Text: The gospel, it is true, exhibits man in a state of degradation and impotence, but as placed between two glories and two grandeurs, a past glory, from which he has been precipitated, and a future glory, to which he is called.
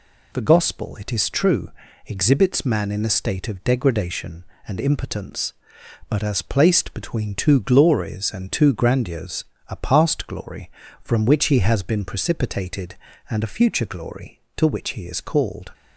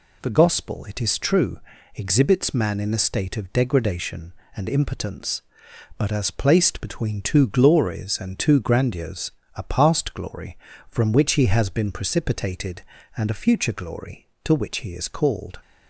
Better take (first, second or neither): neither